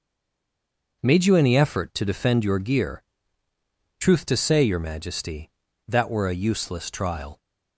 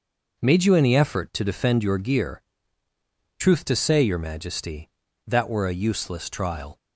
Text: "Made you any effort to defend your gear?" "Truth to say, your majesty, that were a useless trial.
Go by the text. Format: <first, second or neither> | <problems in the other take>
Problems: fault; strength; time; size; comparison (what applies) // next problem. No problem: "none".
second | stays silent before the first word; until 1.0 s; 1.0 s long